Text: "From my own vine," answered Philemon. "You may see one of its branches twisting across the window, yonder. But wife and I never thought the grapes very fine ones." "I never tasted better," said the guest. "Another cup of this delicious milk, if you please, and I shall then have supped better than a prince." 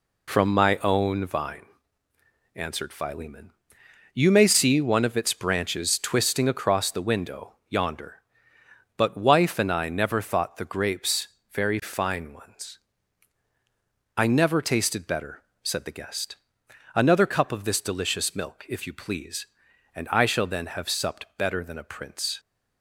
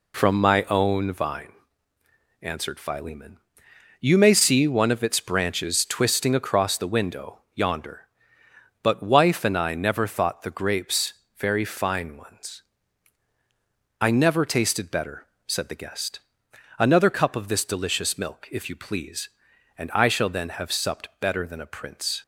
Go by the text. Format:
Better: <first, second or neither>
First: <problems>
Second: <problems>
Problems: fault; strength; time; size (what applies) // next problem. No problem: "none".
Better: neither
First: pauses between "grapes" and "very"; slight; at 11.2 s; 0.22 s long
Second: pauses between "grapes" and "very"; slight; at 11.1 s; 0.22 s long